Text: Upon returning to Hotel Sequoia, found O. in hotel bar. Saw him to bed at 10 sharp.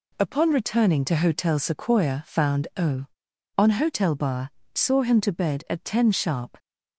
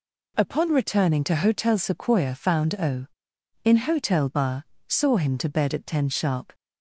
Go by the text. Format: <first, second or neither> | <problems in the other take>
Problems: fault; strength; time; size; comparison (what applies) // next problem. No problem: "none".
second | says "on" for "in"; at 3.5 s